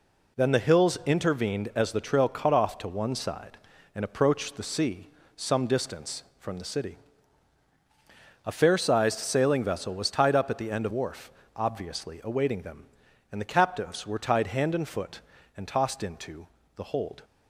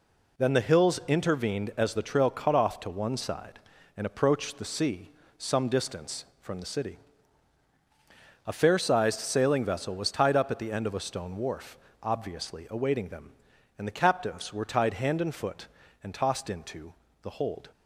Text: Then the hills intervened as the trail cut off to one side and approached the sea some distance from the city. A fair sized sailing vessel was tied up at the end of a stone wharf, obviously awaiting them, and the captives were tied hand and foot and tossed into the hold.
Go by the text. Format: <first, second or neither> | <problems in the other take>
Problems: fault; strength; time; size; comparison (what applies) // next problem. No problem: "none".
second | pauses between "sea" and "some"; slight; at 5.0 s; 0.26 s long; slight in the second // skips "a stone"; at 10.9 s // pauses between "into" and "the"; slight; at 16.4 s; 0.28 s long; slight in the second